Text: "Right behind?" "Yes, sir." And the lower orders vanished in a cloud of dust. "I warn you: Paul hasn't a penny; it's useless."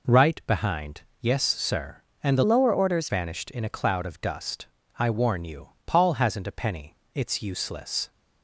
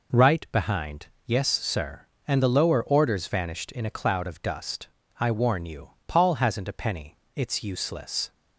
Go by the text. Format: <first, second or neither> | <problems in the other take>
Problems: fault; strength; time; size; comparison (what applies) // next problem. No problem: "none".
second | changes voice from "lower" to "orders"; from 2.4 to 3.0 s; 0.6 s long